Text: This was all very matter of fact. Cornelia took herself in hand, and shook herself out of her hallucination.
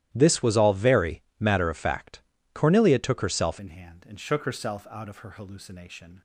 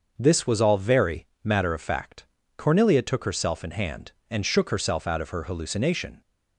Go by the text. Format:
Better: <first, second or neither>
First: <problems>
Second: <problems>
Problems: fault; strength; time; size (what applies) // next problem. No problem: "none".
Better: second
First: starts louder than the rest; strong; until 1.1 s; 13 dB // pauses between "very" and "matter"; slight; at 1.2 s; 0.18 s long // changes voice at "in"; from 3.5 s on; 2.7 s long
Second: starts louder than the rest; until 1.1 s; 6 dB // pauses between "very" and "matter"; slight; at 1.2 s; 0.18 s long